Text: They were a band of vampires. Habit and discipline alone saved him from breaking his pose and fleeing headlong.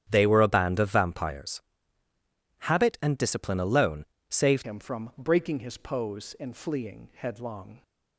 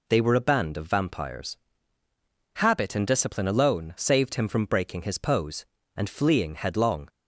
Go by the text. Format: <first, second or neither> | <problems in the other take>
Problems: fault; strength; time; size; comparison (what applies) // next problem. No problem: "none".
second | starts louder than the rest; strong; until 1.1 s; 9.5 dB // pauses between "alone" and "saved"; slight; at 4.0 s; 0.24 s long // changes voice at "him"; from 4.6 s on; 3.2 s long